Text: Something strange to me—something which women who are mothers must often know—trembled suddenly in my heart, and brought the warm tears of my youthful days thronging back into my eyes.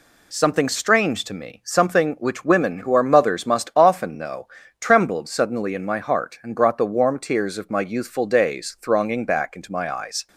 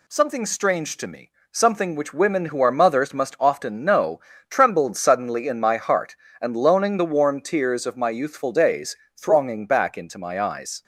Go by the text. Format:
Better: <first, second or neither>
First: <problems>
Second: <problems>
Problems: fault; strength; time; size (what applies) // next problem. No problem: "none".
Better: first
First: none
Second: says "loaning" for "brought"; at 6.5 s // pauses between "days" and "thronging"; slight; at 8.9 s; 0.18 s long